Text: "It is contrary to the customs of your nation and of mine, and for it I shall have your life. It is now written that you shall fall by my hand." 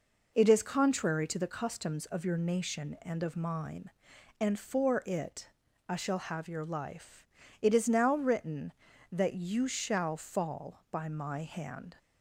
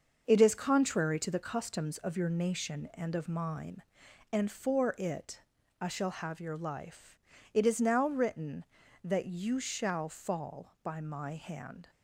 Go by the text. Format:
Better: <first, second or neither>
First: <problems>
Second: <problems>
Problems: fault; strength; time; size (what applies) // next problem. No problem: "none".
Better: first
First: pauses between "it" and "I"; at 5.4 s; 0.38 s long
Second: gets quieter; throughout; 7 dB // pauses between "it" and "I"; at 5.4 s; 0.38 s long